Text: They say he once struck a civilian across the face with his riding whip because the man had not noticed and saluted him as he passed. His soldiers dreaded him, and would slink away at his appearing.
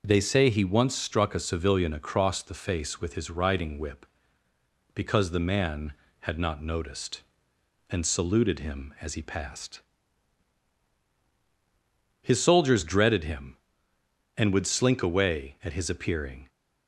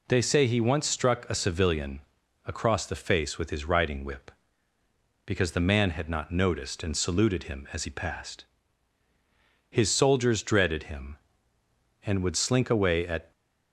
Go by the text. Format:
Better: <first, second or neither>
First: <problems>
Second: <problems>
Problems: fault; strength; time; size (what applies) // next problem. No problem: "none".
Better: first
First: none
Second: pauses between "civilian" and "across"; at 2.0 s; 0.44 s long // stops before "his appearing"; at 13.3 s